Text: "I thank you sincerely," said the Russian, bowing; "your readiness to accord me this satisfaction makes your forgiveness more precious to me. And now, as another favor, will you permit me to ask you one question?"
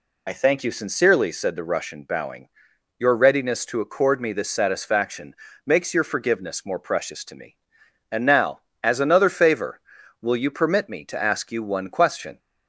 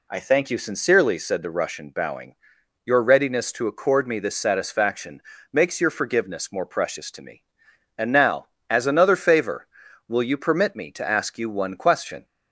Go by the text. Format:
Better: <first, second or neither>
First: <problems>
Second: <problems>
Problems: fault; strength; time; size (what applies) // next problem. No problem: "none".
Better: second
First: loses the start of "I"; at 0.2 s; 35 ms // pauses between "satisfaction" and "makes"; slight; at 5.3 s; 0.32 s long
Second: pauses between "satisfaction" and "makes"; slight; at 5.2 s; 0.32 s long